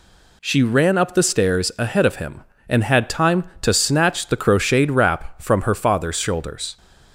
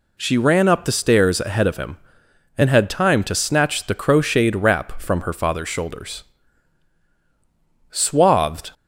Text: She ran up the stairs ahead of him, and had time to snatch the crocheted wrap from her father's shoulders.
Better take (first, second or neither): first